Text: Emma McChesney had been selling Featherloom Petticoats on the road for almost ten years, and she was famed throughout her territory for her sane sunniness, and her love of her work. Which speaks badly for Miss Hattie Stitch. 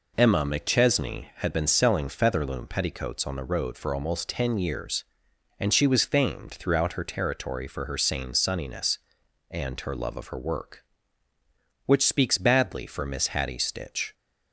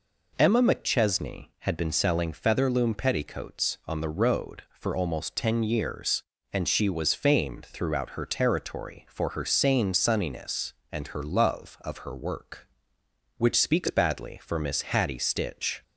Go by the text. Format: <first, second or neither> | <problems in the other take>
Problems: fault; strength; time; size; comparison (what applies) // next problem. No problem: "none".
neither | none